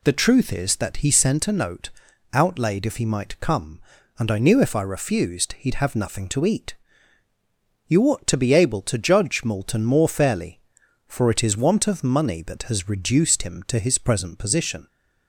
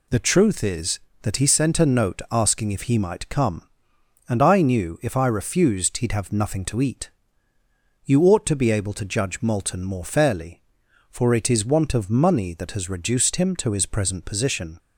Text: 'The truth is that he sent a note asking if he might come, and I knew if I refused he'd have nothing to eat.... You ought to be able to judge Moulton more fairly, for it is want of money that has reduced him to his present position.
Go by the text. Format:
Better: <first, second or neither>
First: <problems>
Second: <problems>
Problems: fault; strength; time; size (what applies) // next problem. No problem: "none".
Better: second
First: says "outlaid" for "asking"; at 2.3 s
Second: none